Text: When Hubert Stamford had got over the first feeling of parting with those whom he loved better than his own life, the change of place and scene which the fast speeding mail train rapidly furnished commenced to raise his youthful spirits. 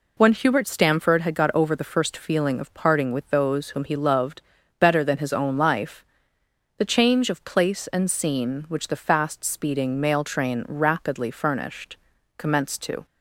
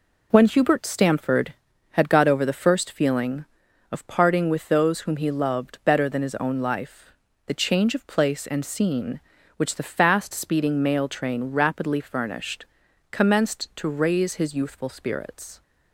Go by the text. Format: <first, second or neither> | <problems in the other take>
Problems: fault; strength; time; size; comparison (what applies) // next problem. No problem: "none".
second | pauses between "loved" and "better"; at 4.4 s; 0.38 s long // pauses between "furnished" and "commenced"; at 11.9 s; 0.40 s long; also in the second // stops before "raise his youthful spirits"; at 13.0 s